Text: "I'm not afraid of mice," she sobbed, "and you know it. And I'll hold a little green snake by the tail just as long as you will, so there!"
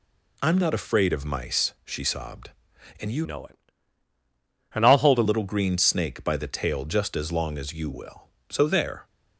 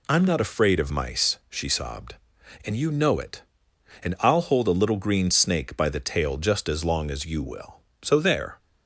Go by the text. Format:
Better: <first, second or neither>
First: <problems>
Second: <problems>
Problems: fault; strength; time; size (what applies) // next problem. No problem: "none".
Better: second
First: changes voice from "know" to "a"; from 3.2 to 5.2 s; 2.0 s long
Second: none